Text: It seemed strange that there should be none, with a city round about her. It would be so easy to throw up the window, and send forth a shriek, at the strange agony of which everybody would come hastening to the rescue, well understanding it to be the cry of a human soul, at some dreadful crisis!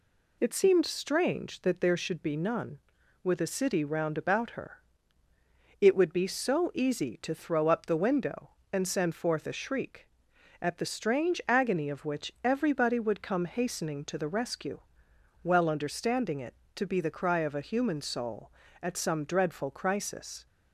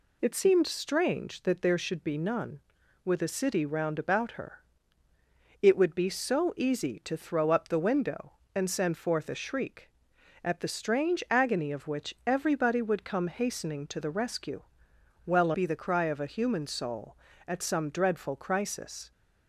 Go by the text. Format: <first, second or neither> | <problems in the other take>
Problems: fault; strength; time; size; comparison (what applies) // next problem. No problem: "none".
first | skips "understanding it to"; at 15.5 s